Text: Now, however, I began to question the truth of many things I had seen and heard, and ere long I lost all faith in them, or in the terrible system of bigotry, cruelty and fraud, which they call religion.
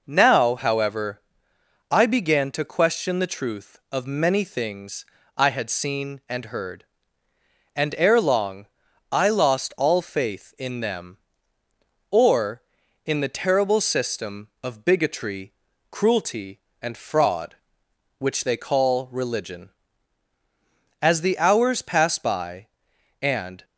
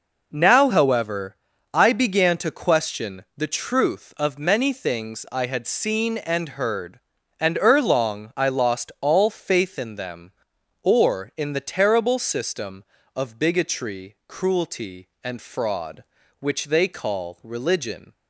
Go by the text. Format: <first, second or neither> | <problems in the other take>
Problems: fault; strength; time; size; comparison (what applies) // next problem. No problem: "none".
second | pauses between "things" and "I"; slight; at 5.0 s; 0.32 s long // pauses between "long" and "I"; noticeable; at 8.6 s; 0.46 s long // goes on to say "As the hours passed by and"; strong; from 21.0 s on; 2.6 s long